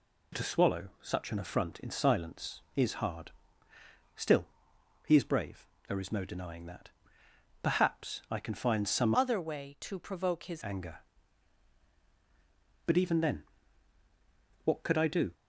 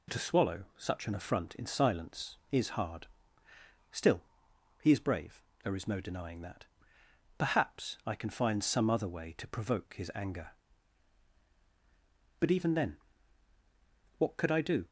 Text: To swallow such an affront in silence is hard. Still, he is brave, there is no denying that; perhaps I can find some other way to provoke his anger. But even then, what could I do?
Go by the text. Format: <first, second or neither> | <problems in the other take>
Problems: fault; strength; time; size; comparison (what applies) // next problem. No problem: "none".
second | changes voice from "other" to "his"; from 9.1 to 10.6 s; 1.5 s long